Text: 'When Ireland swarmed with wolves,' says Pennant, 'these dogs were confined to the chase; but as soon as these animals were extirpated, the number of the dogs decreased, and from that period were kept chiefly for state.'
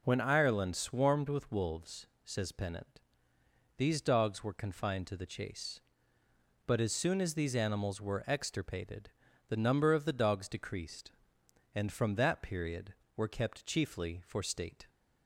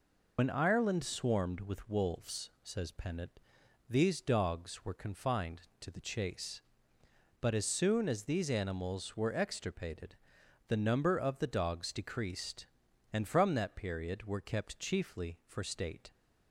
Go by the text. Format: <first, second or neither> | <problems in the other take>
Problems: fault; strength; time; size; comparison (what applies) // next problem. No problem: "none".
first | loses the start of "When"; at 0.3 s; 65 ms